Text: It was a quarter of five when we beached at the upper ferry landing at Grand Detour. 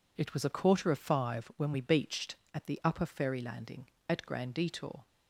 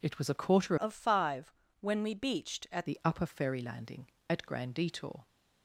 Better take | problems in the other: first | changes voice from "of" to "at"; from 0.7 to 2.8 s; 2.1 s long // pauses between "five" and "when"; slight; at 1.5 s; 0.28 s long

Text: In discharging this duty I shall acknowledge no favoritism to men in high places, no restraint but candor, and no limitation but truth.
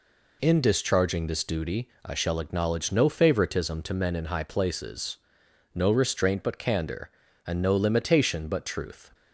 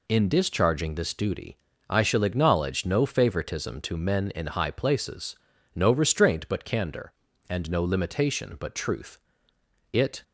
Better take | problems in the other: first | pauses between "duty" and "I"; slight; at 1.5 s; 0.32 s long; slight in the first // goes on to say "It"; slight; from 9.9 s on; 0.32 s long

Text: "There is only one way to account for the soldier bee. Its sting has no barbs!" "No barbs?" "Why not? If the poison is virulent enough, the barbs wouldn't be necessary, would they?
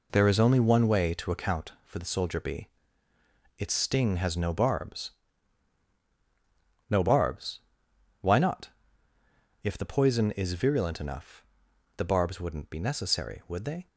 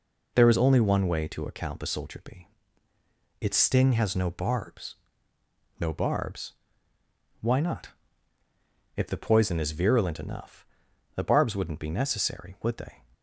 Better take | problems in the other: first | skips "for"; at 1.8 s

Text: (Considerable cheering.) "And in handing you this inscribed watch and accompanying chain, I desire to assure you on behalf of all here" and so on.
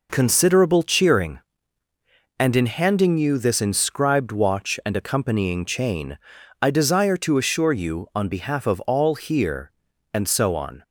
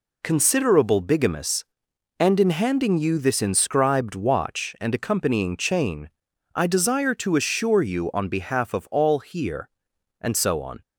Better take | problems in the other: first | says "bigamous" for "cheering"; at 0.9 s

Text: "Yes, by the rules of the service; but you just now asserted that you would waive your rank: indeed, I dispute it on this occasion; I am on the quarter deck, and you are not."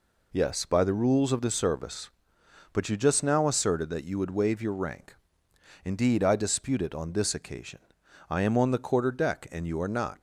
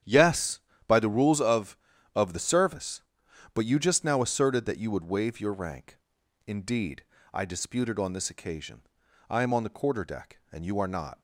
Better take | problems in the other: first | starts louder than the rest; strong; until 1.3 s; 9.5 dB // says "of" twice; at 2.1 s

